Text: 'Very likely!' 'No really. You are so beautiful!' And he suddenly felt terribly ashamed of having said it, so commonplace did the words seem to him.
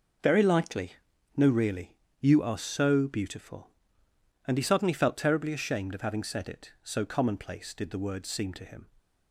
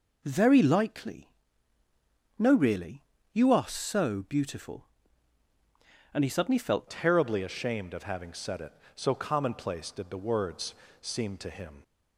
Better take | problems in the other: first | changes voice at "terribly"; from 6.8 s on; 5.0 s long // pauses between "words" and "seem"; slight; at 10.7 s; 0.26 s long

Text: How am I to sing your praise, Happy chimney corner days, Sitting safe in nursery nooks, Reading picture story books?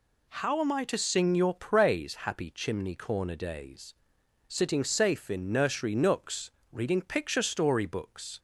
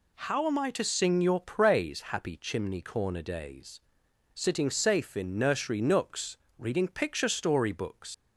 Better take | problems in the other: first | leaves "books" unfinished; at 8.1 s; 105 ms

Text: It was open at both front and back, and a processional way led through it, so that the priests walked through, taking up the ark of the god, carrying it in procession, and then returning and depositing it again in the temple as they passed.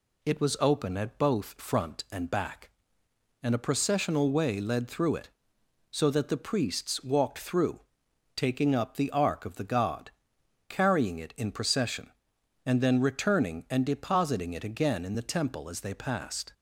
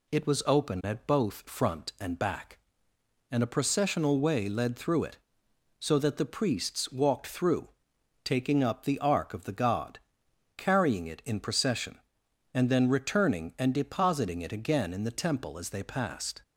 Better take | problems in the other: neither | none

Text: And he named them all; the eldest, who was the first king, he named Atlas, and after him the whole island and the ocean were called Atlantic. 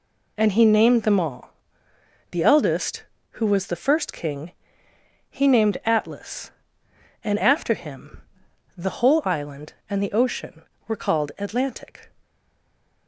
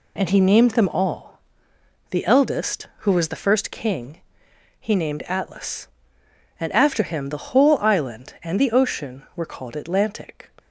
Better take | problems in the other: second | pauses between "him" and "the"; noticeable; at 8.2 s; 0.52 s long // stays silent after the last word; slight; from 12.2 s on; 0.8 s long

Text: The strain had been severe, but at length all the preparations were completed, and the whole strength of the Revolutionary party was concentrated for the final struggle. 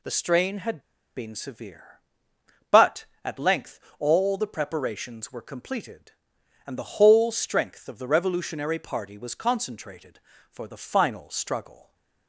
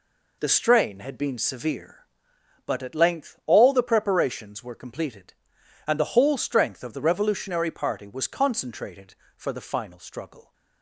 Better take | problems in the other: second | pauses between "had" and "been"; at 0.7 s; 0.37 s long // pauses between "length" and "all"; slight; at 3.7 s; 0.20 s long

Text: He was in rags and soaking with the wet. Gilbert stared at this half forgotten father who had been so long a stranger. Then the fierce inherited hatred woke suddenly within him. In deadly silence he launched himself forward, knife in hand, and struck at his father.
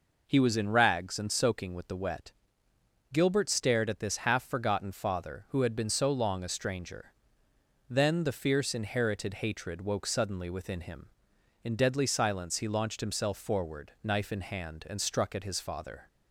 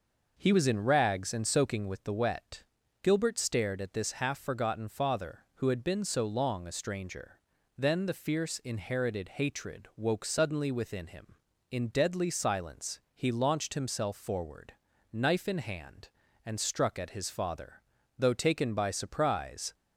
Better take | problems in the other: first | goes on to say "Though taken by surprise"; from 18.1 s on; 1.5 s long

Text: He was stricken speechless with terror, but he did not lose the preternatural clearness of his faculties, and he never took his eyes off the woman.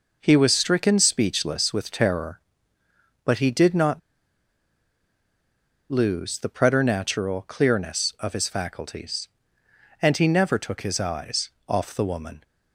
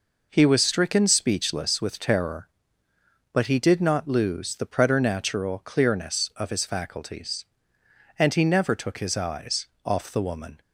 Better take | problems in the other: second | pauses between "not" and "lose"; strong; at 4.0 s; 1.9 s long // pauses between "eyes" and "off"; slight; at 11.5 s; 0.18 s long; slight in the second

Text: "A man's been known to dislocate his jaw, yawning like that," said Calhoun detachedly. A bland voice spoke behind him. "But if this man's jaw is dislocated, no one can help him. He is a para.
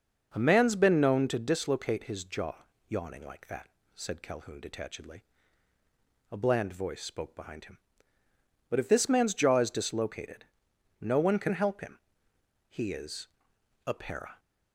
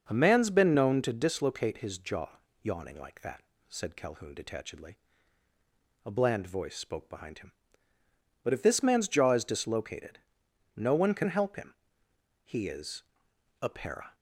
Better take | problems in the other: neither | pauses between "is" and "a"; noticeable; the same in both

